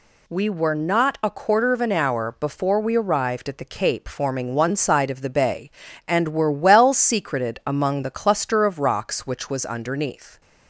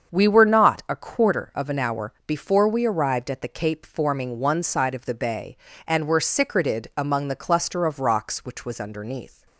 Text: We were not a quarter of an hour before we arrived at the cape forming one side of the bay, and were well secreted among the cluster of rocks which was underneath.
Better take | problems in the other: first | starts louder than the rest; until 1.2 s; 7 dB // skips "well"; at 6.1 s

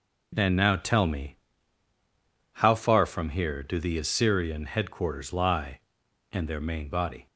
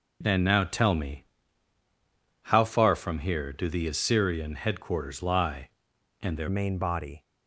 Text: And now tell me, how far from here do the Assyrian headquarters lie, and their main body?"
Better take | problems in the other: first | changes voice at "main"; from 6.4 s on; 0.8 s long

